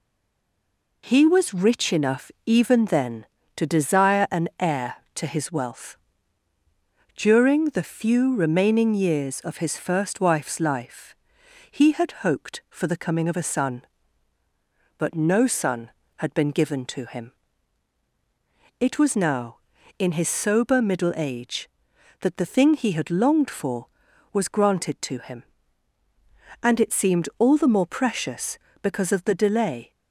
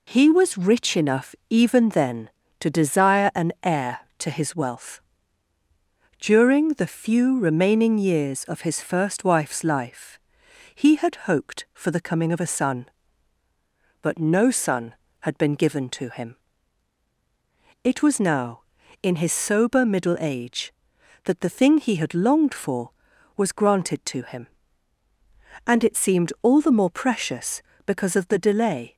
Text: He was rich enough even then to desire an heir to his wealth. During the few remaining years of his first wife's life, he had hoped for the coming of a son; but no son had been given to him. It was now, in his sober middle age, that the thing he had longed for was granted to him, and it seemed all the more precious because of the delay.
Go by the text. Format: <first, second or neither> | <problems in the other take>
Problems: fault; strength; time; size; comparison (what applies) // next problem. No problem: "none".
second | stays silent before the first word; until 1.0 s; 1.0 s long // pauses between "enough" and "even"; slight; at 2.3 s; 0.16 s long; slight in the second